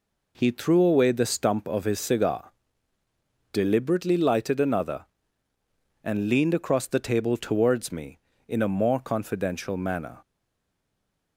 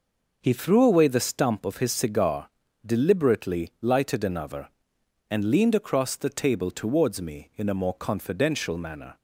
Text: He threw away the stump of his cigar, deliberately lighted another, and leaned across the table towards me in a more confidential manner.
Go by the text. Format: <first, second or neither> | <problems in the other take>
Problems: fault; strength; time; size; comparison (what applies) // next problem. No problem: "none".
second | stays silent after the last word; from 10.2 s on; 1.1 s long